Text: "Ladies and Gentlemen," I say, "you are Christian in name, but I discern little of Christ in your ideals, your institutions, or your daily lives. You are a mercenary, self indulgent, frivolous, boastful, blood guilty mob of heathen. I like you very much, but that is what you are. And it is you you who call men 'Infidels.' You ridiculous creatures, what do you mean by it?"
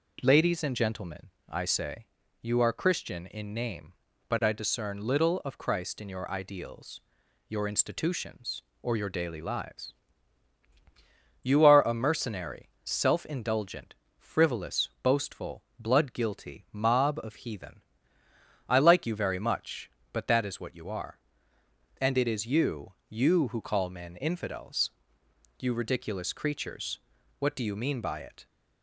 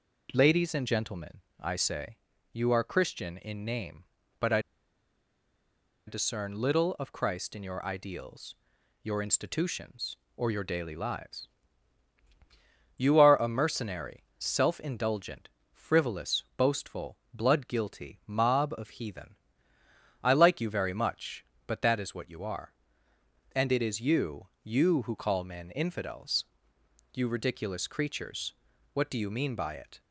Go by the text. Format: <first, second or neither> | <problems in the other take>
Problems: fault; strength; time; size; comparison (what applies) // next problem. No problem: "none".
first | pauses between "I" and "discern"; strong; at 4.6 s; 1.4 s long // pauses between "you" and "you"; slight; at 24.4 s; 0.16 s long; slight in the first